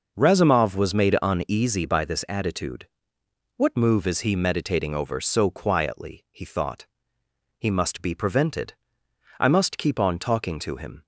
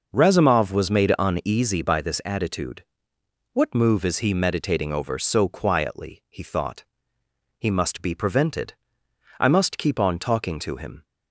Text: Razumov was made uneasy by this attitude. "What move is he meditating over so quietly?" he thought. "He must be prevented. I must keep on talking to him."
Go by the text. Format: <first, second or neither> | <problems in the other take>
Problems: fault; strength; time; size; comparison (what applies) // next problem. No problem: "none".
neither | none